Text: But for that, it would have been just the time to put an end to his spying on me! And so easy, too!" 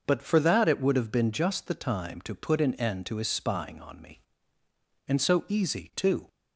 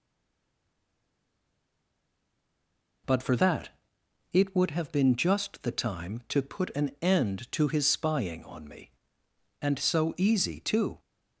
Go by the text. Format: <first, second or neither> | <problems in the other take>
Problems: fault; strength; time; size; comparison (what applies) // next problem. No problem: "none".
first | stays silent before the first word; strong; until 3.0 s; 3.0 s long